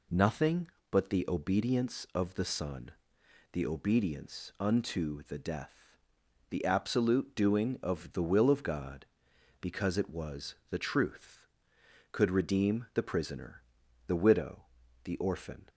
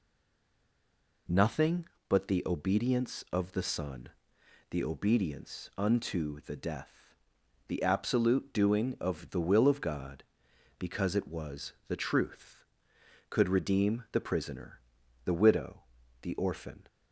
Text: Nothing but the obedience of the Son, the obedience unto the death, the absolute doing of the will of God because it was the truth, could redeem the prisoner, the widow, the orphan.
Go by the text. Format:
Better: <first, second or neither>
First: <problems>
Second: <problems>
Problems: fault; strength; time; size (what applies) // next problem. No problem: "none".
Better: first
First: pauses between "was" and "the"; slight; at 10.5 s; 0.16 s long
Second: stays silent before the first word; noticeable; until 1.2 s; 1.2 s long // pauses between "was" and "the"; slight; at 11.7 s; 0.16 s long